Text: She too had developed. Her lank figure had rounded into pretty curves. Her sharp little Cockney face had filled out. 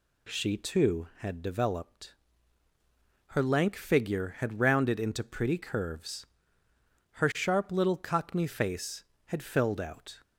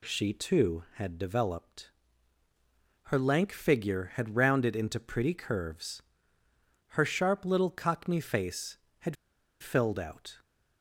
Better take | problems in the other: first | pauses between "had" and "filled"; at 9.1 s; 0.45 s long

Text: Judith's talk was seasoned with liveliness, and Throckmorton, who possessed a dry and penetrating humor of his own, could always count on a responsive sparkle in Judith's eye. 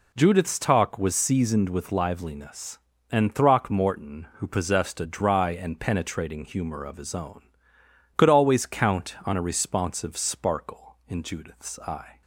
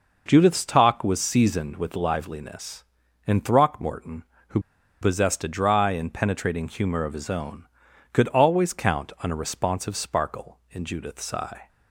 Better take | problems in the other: first | pauses between "who" and "possessed"; at 4.5 s; 0.42 s long

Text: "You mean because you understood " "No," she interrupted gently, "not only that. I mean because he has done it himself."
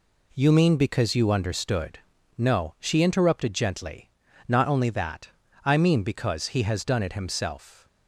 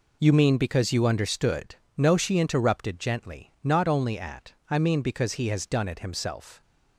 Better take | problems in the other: first | says "at" for "that"; at 4.1 s

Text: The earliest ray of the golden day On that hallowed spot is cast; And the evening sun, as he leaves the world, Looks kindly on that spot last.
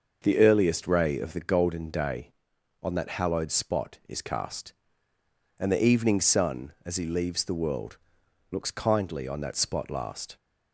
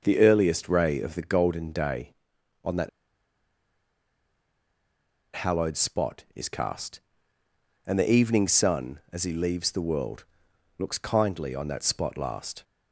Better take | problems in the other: first | starts louder than the rest; noticeable; until 1.0 s; 6 dB; noticeable in the first // pauses between "that" and "hallowed"; strong; at 2.8 s; 2.4 s long

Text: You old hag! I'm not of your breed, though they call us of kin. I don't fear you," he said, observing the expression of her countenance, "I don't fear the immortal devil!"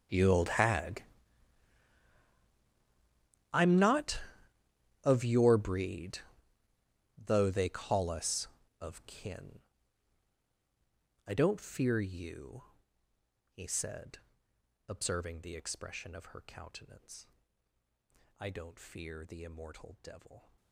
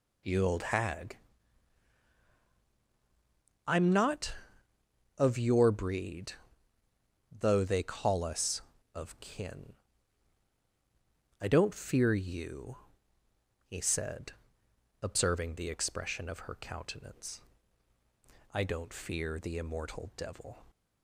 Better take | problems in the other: second | gets quieter; strong; throughout; 22 dB

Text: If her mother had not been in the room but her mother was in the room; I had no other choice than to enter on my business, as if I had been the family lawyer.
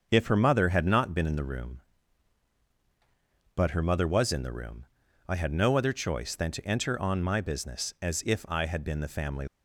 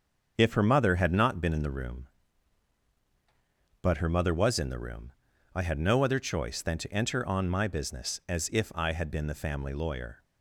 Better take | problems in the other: second | starts louder than the rest; until 1.1 s; 6.5 dB; also in the second // stops before "lawyer"; at 9.4 s

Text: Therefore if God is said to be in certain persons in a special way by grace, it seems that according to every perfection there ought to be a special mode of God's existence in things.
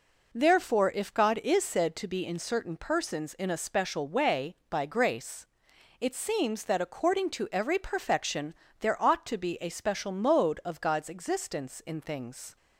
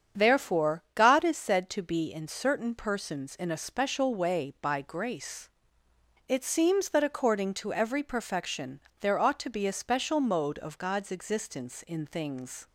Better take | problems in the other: first | starts louder than the rest; strong; until 1.2 s; 7.5 dB // skips "if"; at 0.8 s // pauses between "perfection" and "there"; slight; at 8.8 s; 0.20 s long; slight in the first

